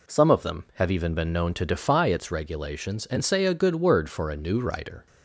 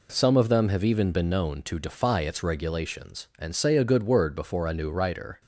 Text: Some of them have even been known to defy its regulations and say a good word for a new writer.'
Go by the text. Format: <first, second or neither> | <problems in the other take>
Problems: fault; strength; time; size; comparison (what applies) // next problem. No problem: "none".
first | says "before" for "for"; at 4.3 s